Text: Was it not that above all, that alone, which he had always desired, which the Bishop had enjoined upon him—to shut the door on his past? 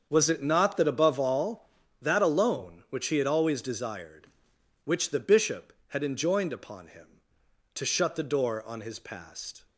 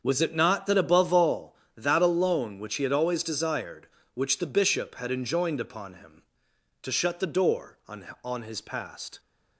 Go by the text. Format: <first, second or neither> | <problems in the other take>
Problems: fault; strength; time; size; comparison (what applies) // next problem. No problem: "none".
first | starts louder than the rest; until 1.0 s; 7 dB; also in the first // says "on" twice; at 8.2 s